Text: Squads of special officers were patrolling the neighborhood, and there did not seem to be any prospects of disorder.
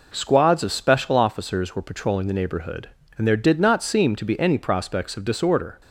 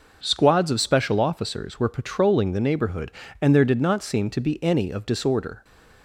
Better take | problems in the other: first | skips "prospects"; at 4.9 s

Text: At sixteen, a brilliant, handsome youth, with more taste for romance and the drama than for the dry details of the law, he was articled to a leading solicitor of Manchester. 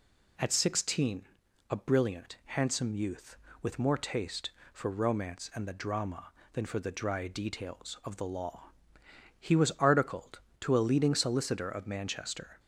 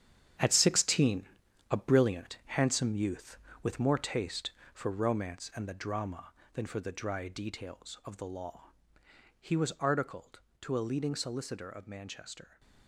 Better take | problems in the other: first | gets quieter; strong; throughout; 11 dB

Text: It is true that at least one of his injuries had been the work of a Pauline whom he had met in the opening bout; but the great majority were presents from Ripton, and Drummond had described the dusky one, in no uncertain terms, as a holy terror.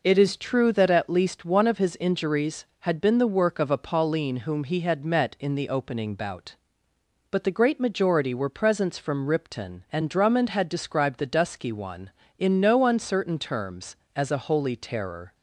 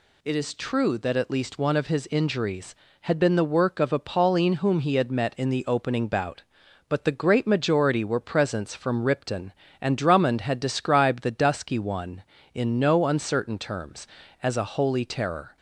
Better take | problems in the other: neither | none

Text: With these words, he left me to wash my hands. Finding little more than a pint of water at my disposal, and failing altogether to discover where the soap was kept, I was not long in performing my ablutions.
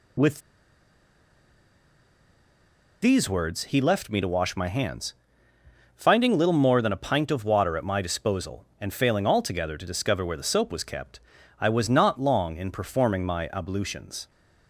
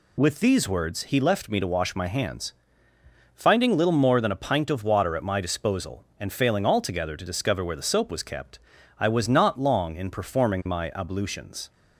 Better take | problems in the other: second | pauses between "With" and "these"; strong; at 0.4 s; 2.6 s long

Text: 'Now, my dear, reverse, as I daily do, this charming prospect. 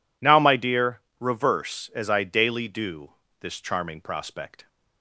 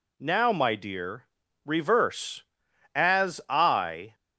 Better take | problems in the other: first | stops before "daily do this charming prospect"; at 4.1 s

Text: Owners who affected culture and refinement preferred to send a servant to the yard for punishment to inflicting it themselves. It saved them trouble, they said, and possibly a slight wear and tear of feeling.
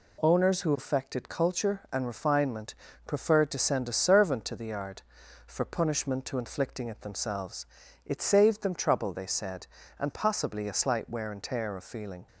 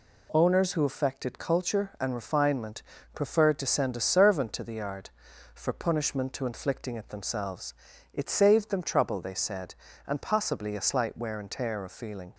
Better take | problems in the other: neither | pauses between "refinement" and "preferred"; slight; the same in both

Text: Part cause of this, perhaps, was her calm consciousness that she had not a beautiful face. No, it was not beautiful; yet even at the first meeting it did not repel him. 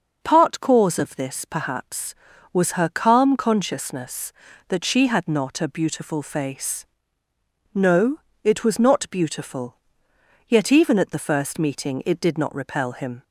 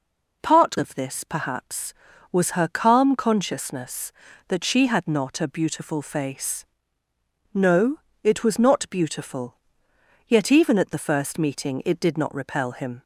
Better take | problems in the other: first | skips "cause"; at 0.7 s

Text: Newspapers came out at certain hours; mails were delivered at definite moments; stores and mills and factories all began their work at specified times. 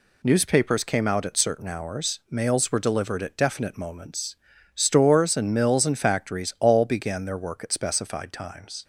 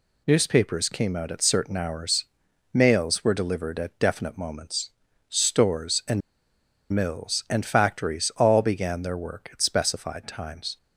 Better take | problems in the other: first | pauses between "and" and "mills"; noticeable; at 6.2 s; 0.72 s long

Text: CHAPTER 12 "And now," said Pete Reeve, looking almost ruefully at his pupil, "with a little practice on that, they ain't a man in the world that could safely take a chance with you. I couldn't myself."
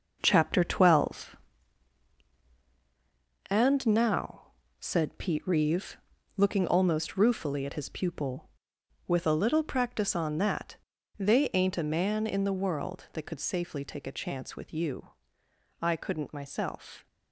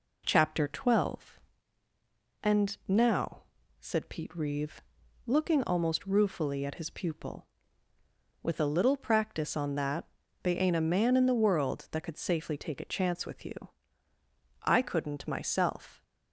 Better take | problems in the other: second | gets quieter; strong; throughout; 7.5 dB

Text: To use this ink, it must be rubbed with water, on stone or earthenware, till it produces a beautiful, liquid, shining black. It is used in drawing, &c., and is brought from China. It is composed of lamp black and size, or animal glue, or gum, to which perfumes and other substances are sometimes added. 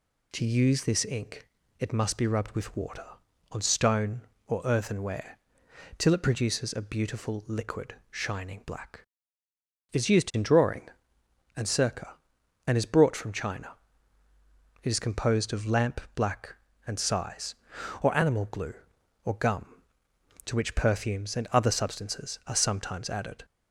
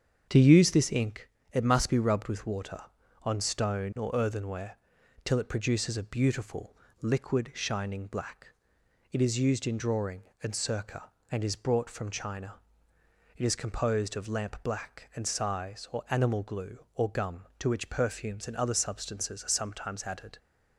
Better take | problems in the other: first | starts louder than the rest; strong; until 1.4 s; 7.5 dB

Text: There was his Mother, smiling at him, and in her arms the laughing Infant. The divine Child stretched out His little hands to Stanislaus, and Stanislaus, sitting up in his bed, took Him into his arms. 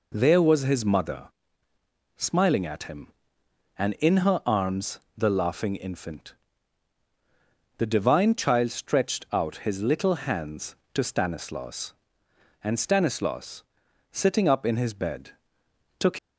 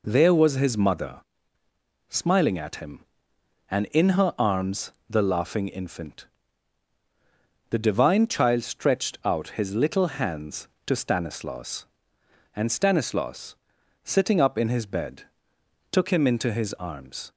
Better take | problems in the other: second | pauses between "arms" and "the"; slight; at 4.9 s; 0.18 s long; slight in the second // stops before "Him into his arms"; at 16.1 s

